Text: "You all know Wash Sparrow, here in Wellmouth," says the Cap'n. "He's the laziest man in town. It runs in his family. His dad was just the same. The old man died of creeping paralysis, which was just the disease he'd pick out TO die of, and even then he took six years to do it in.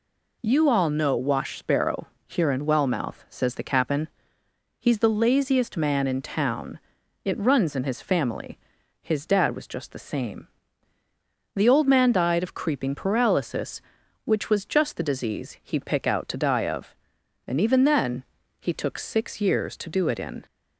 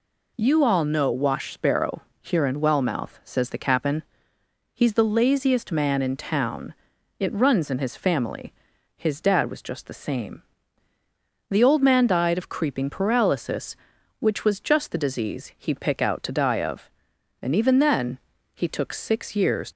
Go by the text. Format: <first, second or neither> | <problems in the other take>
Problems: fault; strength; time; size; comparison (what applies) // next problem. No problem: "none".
first | pauses between "then" and "he"; at 18.1 s; 0.38 s long; also in the first // stops before "to do it in"; at 19.7 s